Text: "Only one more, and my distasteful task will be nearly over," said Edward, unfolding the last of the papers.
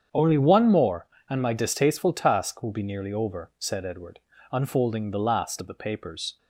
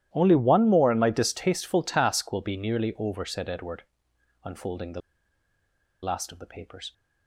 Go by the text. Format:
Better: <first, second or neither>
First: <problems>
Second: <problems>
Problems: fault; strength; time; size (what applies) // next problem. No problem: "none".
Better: first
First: starts louder than the rest; strong; until 1.3 s; 8 dB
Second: starts louder than the rest; strong; until 1.1 s; 12.5 dB // pauses between "the" and "last"; at 5.0 s; 1.0 s long